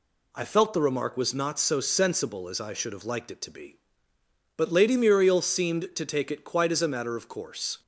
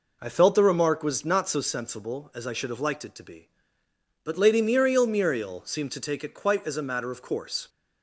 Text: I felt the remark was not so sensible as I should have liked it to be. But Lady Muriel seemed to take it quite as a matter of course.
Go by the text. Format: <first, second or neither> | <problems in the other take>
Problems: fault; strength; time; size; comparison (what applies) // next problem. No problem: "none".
first | says "Muriel" twice; at 5.0 s